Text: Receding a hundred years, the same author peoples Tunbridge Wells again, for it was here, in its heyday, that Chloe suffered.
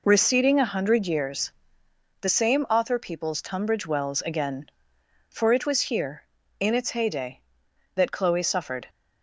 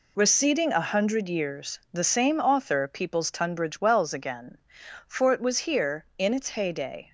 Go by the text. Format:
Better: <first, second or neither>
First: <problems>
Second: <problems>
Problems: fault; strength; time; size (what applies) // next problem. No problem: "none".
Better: first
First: none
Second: stops before "that Chloe suffered"; at 7.0 s